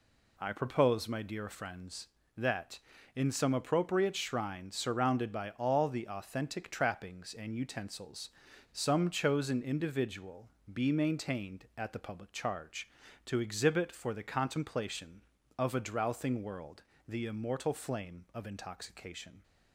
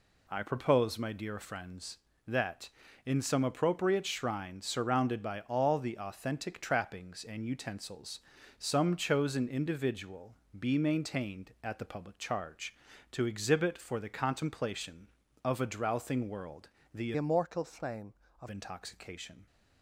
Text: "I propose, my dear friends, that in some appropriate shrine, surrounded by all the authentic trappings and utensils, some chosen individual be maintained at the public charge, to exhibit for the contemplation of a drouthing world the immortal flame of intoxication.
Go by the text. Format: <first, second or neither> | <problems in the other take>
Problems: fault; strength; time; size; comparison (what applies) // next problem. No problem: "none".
first | pauses between "individual" and "be"; slight; at 10.3 s; 0.22 s long; slight in the first // pauses between "world" and "the"; slight; at 16.6 s; 0.24 s long; slight in the first // changes voice from "immortal" to "of"; from 17.1 to 18.4 s; 1.3 s long